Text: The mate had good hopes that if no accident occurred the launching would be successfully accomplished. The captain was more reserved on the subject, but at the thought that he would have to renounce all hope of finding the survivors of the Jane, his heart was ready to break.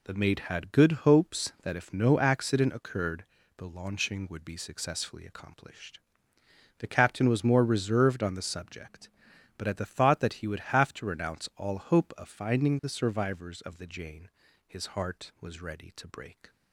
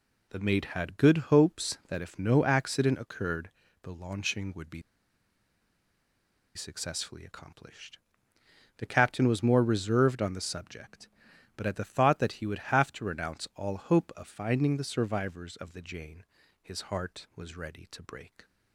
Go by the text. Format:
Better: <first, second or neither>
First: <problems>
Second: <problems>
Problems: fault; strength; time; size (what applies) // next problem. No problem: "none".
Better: first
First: pauses between "occurred" and "the"; slight; at 3.2 s; 0.34 s long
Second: pauses between "occurred" and "the"; slight; at 3.4 s; 0.34 s long // pauses between "be" and "successfully"; strong; at 4.8 s; 1.7 s long